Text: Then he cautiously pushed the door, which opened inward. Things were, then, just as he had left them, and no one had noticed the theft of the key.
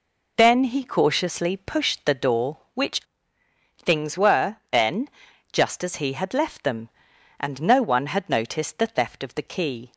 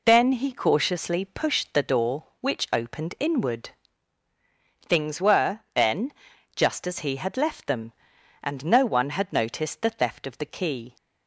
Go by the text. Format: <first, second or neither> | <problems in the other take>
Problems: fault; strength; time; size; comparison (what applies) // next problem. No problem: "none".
second | skips "opened inward"; at 3.4 s